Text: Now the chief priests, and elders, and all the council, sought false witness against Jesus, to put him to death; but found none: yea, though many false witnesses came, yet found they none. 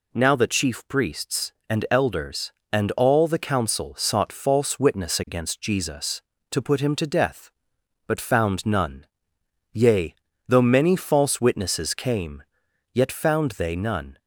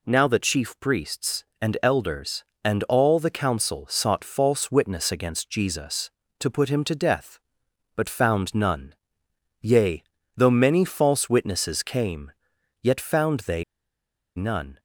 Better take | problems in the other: first | pauses between "they" and "none"; noticeable; at 13.6 s; 0.73 s long

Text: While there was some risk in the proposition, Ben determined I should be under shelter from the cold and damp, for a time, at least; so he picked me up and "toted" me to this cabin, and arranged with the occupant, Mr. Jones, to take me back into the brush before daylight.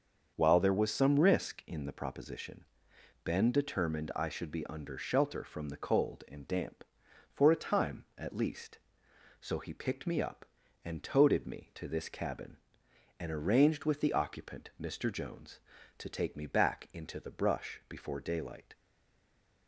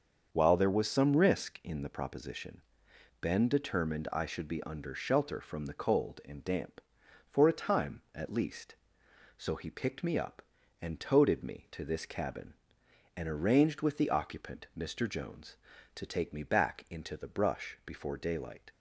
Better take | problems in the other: second | starts louder than the rest; until 1.3 s; 6.5 dB; also in the second // stays silent after the last word; slight; from 18.7 s on; 0.9 s long

